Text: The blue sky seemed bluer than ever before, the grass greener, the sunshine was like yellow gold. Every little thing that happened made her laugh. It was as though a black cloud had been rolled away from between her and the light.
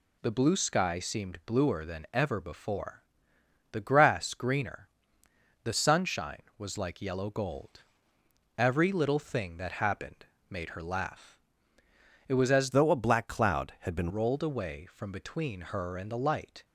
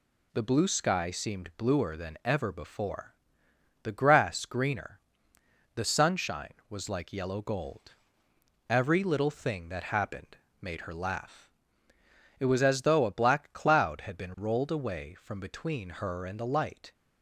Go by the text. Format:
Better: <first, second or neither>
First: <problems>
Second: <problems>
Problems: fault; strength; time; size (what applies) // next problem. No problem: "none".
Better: second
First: pauses between "happened" and "made"; slight; at 10.2 s; 0.24 s long // changes voice from "though" to "been"; from 12.7 to 14.1 s; 1.4 s long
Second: pauses between "happened" and "made"; slight; at 10.3 s; 0.24 s long